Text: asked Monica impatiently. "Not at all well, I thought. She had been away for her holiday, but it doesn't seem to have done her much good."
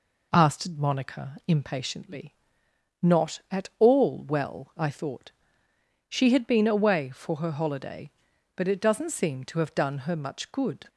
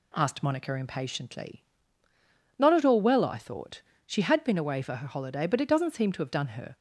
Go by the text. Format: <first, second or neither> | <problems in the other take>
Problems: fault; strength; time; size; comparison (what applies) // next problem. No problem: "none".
first | stops before "much good"; at 6.7 s